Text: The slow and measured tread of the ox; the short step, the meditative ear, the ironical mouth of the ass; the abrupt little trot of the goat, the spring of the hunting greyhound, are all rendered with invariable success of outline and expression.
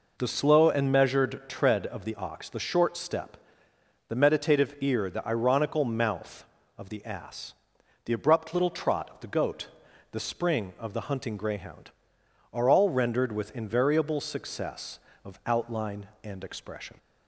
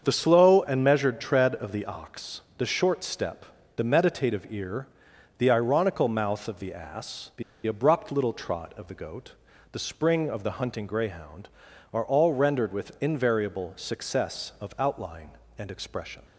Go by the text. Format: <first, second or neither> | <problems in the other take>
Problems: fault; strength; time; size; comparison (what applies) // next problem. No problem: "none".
first | starts louder than the rest; until 1.0 s; 7 dB // pauses between "the" and "abrupt"; slight; at 7.4 s; 0.24 s long